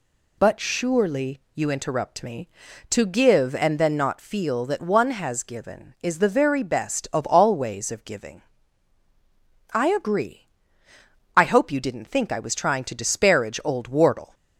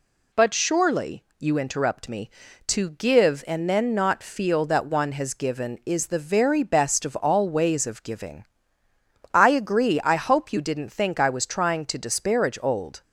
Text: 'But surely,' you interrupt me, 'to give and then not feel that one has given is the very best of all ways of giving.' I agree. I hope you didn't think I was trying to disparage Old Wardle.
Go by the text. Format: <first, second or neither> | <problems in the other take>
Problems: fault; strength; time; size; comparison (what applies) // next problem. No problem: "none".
first | stops before "Wardle"; at 13.0 s